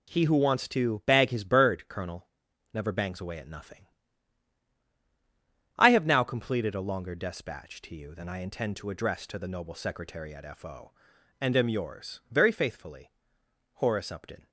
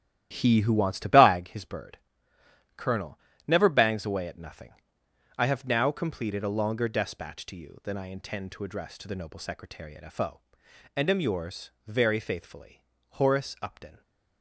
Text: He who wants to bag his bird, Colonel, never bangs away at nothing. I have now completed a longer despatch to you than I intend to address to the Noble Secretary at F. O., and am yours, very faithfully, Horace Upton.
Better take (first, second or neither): first